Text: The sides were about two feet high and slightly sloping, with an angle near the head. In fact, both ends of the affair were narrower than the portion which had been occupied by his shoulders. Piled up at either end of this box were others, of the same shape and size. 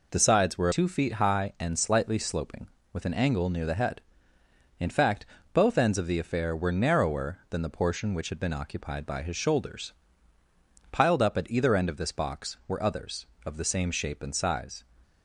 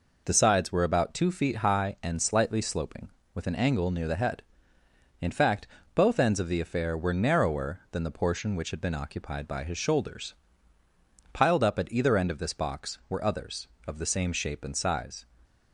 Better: second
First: skips "about"; at 0.7 s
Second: none

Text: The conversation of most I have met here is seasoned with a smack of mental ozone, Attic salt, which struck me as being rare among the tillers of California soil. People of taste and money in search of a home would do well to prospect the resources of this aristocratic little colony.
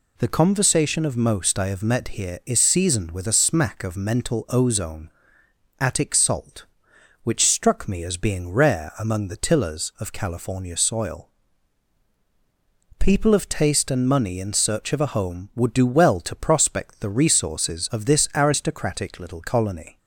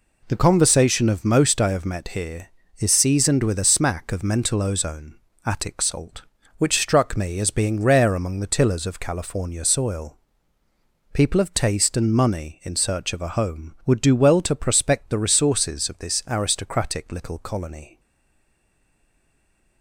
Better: first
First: none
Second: stays silent after the last word; noticeable; from 17.9 s on; 1.9 s long

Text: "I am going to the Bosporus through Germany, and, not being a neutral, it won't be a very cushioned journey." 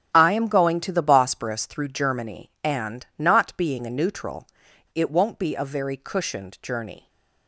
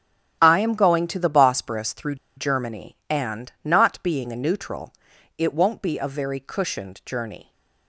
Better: first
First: starts louder than the rest; strong; until 1.1 s; 9.5 dB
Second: starts louder than the rest; strong; until 1.4 s; 10.5 dB // pauses between "through" and "Germany"; slight; at 2.1 s; 0.21 s long

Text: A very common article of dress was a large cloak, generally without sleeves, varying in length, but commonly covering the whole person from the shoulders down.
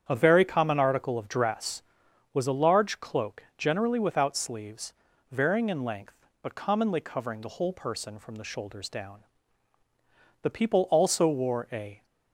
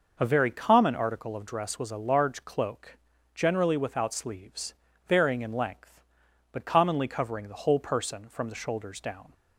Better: second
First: starts louder than the rest; strong; until 1.0 s; 8.5 dB // goes on to say "The people also wore a"; from 10.4 s on; 1.6 s long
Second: none

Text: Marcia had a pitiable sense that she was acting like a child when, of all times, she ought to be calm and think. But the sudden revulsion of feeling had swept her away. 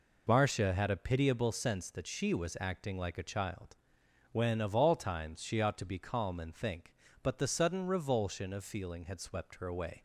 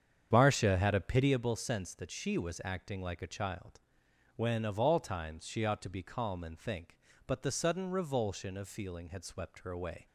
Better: first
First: pauses between "child" and "when"; noticeable; at 3.7 s; 0.56 s long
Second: starts louder than the rest; strong; until 1.4 s; 8 dB // pauses between "child" and "when"; noticeable; at 3.7 s; 0.56 s long

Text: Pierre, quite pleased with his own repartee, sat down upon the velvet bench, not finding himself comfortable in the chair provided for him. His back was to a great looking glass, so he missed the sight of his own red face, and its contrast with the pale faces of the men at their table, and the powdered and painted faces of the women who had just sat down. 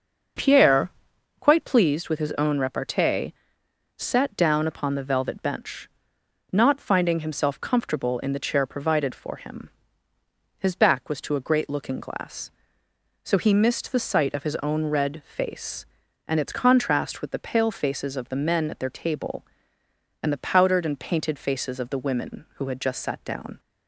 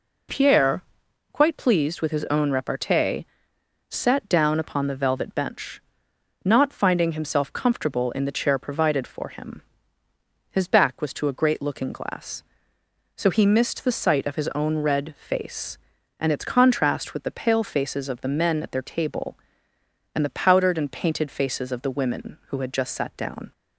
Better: second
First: starts louder than the rest; until 2.0 s; 6.5 dB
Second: none

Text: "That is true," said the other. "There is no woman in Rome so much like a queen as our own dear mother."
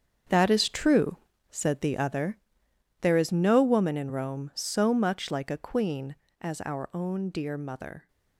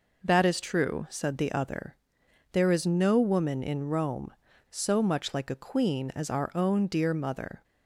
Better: second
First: gets quieter; strong; throughout; 11 dB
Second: none

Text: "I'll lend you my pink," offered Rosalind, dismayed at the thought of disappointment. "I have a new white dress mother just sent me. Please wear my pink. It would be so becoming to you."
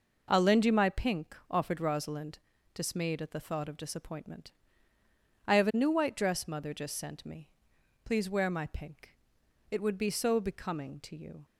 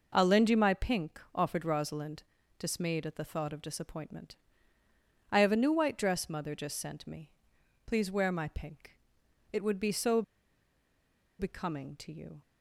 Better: first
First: none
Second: pauses between "so" and "becoming"; at 10.2 s; 1.1 s long

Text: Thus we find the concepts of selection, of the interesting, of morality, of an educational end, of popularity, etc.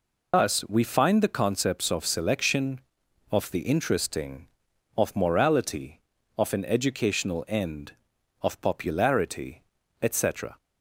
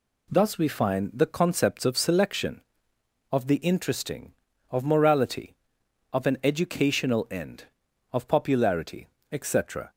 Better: second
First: loses the start of "Thus"; at 0.3 s; 130 ms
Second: none

